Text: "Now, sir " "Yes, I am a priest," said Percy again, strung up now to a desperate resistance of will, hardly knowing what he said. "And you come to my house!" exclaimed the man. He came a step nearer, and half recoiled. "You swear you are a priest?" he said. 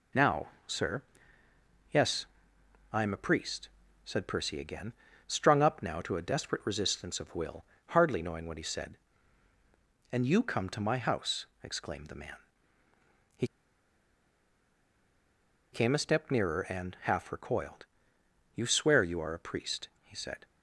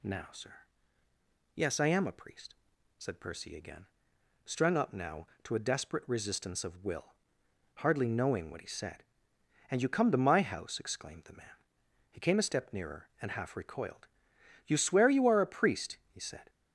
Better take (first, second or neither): second